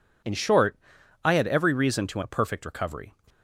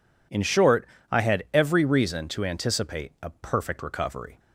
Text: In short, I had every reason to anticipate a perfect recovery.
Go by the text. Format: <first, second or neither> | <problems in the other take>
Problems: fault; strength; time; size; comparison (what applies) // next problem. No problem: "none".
second | skips "anticipate"; at 2.2 s